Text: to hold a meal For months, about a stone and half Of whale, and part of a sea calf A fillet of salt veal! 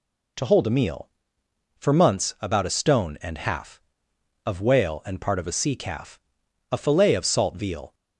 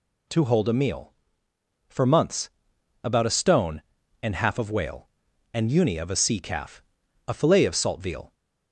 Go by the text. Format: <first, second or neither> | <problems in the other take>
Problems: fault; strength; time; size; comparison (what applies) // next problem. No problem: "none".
first | says "uni" for "part"; at 5.6 s // pauses between "calf" and "A"; noticeable; at 6.8 s; 0.46 s long; noticeable in the first